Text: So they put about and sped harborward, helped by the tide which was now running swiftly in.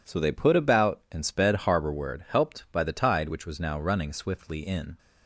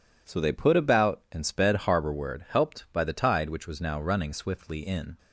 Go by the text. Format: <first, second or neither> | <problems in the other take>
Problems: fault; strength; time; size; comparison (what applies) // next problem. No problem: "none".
neither | none